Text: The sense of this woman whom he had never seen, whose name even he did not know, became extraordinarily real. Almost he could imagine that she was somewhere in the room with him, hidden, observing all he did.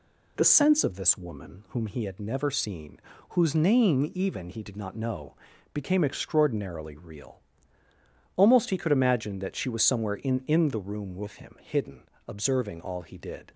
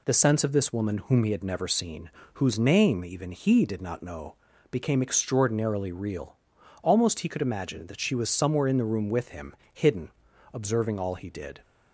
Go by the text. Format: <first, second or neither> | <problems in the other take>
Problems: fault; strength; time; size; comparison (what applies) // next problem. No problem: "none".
second | says "in" twice; at 10.4 s